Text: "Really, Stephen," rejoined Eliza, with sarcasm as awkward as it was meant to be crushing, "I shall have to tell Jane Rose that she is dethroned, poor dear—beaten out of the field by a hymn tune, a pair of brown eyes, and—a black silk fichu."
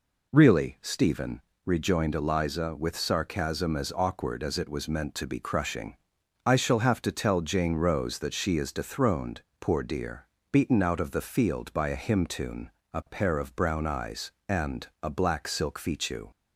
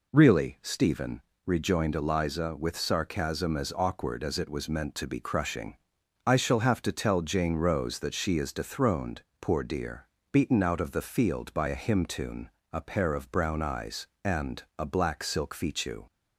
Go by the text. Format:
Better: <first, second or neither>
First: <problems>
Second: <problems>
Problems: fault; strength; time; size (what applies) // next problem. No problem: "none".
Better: neither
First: none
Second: none